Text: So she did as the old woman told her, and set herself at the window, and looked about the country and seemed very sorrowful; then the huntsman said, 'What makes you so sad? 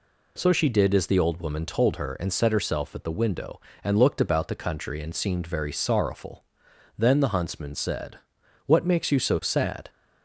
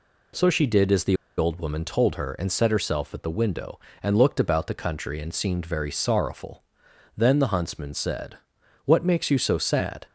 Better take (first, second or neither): first